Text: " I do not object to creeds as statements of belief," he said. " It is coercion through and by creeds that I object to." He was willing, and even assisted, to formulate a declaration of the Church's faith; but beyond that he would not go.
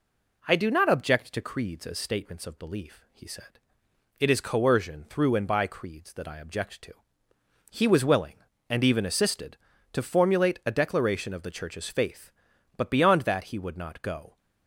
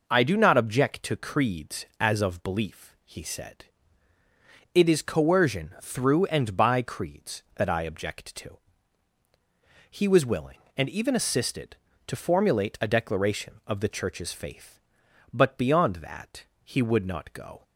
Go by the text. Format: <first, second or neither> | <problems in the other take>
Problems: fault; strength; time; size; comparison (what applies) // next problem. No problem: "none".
first | skips "statements"; at 2.2 s // pauses between "that" and "he"; slight; at 16.4 s; 0.18 s long